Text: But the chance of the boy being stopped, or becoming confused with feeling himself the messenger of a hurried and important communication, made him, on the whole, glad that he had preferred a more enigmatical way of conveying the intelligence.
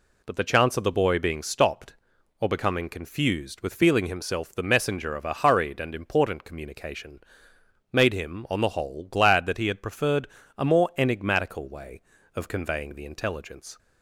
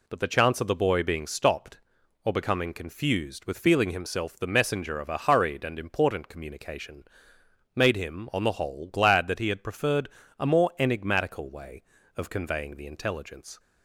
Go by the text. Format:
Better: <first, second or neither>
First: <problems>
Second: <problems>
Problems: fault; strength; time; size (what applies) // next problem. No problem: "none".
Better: neither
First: pauses between "preferred" and "a"; slight; at 10.2 s; 0.28 s long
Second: pauses between "preferred" and "a"; slight; at 10.0 s; 0.28 s long